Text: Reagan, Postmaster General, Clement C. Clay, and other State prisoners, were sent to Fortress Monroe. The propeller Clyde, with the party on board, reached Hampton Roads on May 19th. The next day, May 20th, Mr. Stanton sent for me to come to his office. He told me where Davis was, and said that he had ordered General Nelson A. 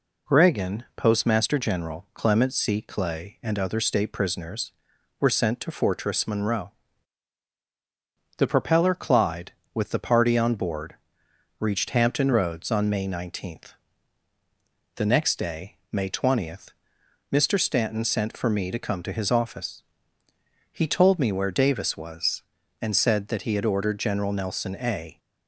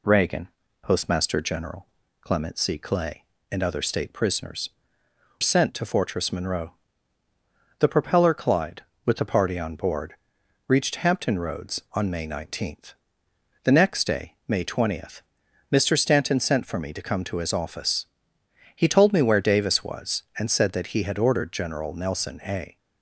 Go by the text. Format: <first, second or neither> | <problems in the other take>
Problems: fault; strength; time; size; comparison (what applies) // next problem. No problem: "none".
first | skips "were"; at 5.0 s